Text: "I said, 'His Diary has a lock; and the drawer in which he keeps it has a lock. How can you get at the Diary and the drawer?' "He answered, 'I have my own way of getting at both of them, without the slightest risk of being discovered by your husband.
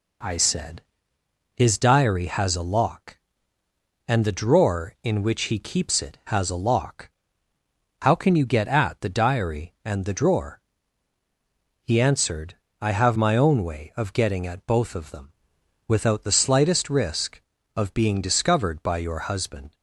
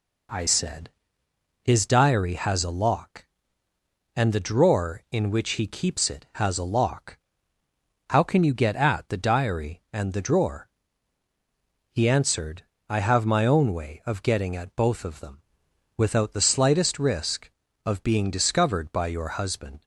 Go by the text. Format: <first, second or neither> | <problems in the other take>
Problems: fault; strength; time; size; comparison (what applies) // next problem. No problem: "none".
neither | none